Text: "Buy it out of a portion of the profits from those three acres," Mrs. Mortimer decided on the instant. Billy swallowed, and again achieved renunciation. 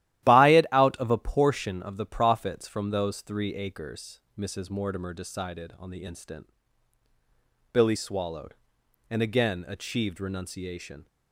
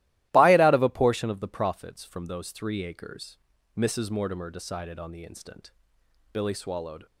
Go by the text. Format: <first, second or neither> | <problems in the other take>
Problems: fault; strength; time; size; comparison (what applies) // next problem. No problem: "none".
first | starts louder than the rest; strong; until 1.3 s; 15.5 dB; strong in the first // stops before "and again achieved renunciation"; at 7.0 s